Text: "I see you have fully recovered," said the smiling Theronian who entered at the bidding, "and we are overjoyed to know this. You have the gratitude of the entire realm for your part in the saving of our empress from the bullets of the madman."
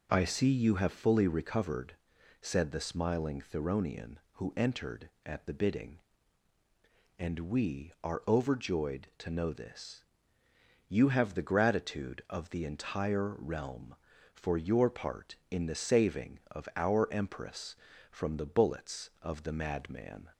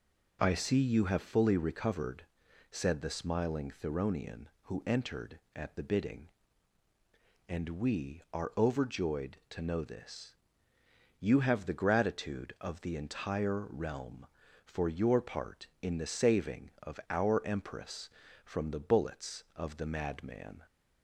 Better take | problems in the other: neither | none

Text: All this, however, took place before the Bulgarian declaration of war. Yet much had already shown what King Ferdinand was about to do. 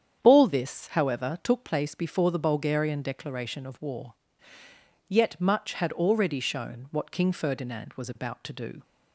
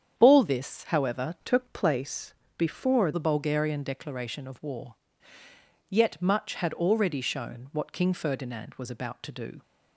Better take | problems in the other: first | starts louder than the rest; strong; until 1.1 s; 8 dB; strong in the first // changes voice from "took" to "before"; from 1.4 to 3.1 s; 1.7 s long // pauses between "place" and "before"; slight; at 2.3 s; 0.24 s long

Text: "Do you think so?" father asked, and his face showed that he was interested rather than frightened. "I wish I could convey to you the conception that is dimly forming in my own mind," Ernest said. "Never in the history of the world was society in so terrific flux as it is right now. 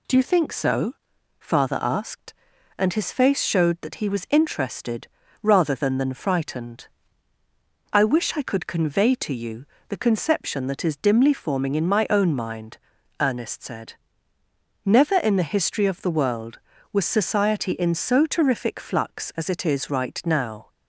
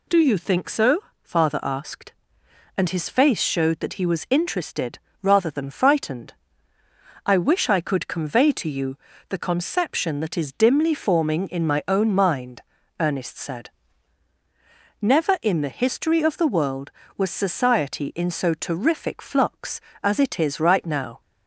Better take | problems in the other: second | pauses between "interested" and "rather"; slight; at 5.0 s; 0.34 s long; slight in the second // says "than" twice; at 5.9 s // pauses between "you" and "the"; slight; at 9.6 s; 0.24 s long; slight in the second

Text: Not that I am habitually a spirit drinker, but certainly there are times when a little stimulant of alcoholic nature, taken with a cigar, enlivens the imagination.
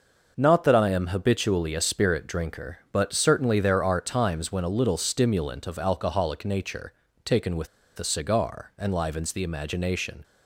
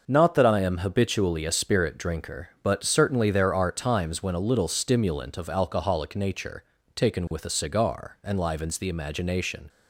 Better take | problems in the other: second | starts louder than the rest; noticeable; until 1.3 s; 6 dB; noticeable in the second // pauses between "with" and "a"; slight; at 7.6 s; 0.31 s long

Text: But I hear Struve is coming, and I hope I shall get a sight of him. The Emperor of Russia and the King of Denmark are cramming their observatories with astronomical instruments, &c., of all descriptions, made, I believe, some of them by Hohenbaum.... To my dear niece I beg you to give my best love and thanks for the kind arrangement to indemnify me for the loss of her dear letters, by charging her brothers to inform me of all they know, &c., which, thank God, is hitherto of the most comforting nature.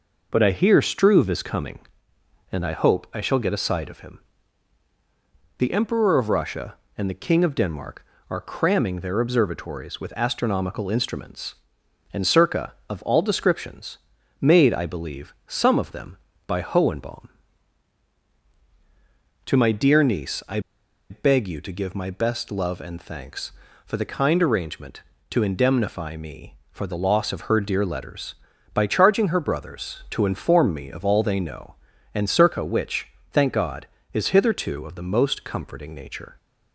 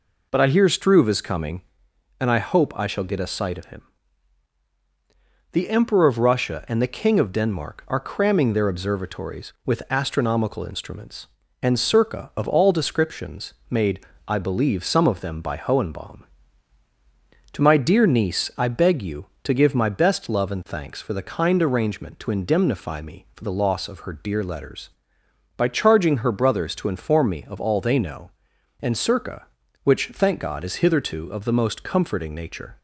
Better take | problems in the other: second | pauses between "I" and "beg"; noticeable; at 20.5 s; 0.50 s long

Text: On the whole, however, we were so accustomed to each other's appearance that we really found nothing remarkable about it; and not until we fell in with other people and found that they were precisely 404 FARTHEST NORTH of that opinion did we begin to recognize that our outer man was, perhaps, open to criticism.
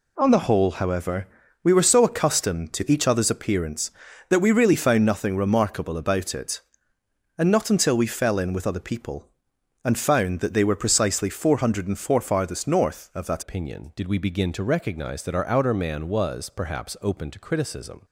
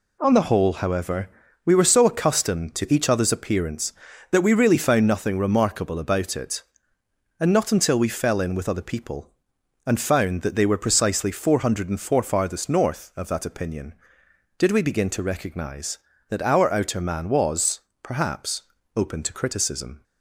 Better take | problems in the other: second | changes voice at "opinion"; from 13.4 s on; 4.6 s long

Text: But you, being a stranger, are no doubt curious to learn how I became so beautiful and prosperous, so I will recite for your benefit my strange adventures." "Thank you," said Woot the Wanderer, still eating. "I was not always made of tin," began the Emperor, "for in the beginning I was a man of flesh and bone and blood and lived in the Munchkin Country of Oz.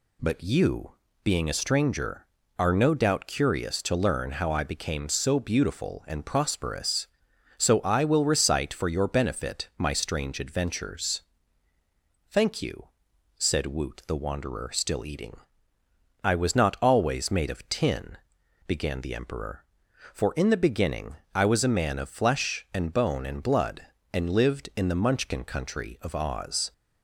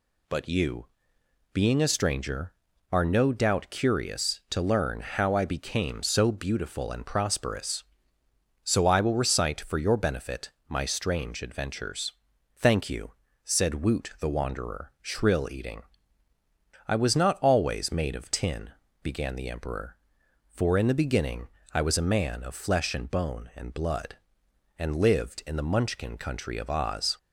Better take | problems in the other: first | pauses between "benefit" and "my"; slight; at 10.4 s; 0.18 s long // says "shrill" for "still"; at 15.0 s // pauses between "beginning" and "I"; slight; at 21.4 s; 0.22 s long; slight in the first

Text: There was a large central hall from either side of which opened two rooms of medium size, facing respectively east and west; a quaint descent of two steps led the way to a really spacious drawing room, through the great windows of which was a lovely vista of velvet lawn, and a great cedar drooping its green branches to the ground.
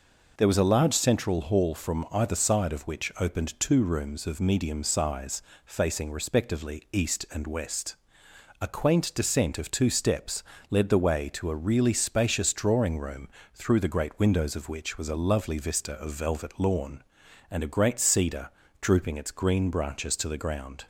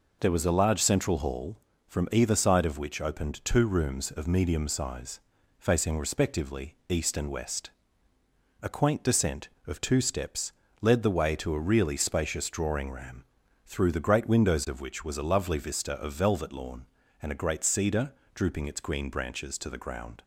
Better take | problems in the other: first | pauses between "steps" and "led"; slight; at 10.5 s; 0.30 s long; slight in the first // says "ram" for "room"; at 12.9 s // pauses between "cedar" and "drooping"; slight; at 18.1 s; 0.22 s long; slight in the first

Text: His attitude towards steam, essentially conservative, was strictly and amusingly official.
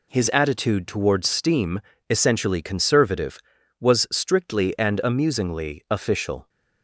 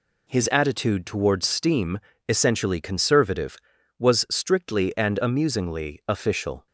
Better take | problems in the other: neither | none

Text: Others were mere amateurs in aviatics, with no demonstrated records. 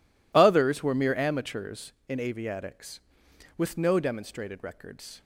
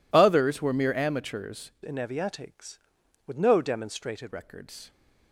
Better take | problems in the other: first | changes voice from "in" to "demonstrated"; from 1.8 to 4.3 s; 2.5 s long

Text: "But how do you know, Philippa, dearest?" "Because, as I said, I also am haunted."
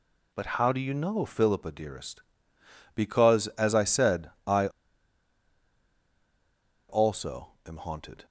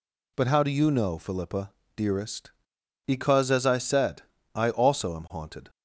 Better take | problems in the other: second | pauses between "I" and "also"; strong; at 4.6 s; 2.2 s long

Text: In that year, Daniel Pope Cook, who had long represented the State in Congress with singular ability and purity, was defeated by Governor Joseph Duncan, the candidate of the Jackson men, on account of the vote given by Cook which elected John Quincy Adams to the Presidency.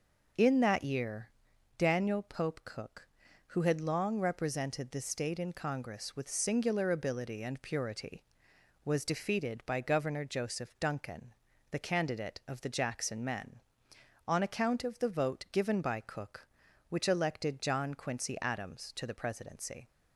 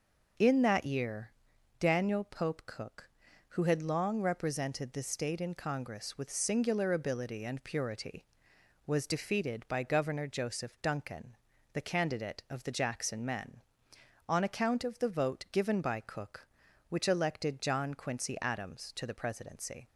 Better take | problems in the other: neither | none

